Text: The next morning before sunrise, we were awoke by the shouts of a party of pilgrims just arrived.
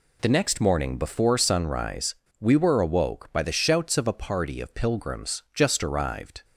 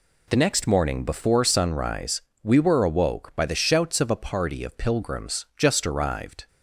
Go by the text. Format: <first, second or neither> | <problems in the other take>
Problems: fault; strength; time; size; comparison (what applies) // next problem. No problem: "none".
neither | none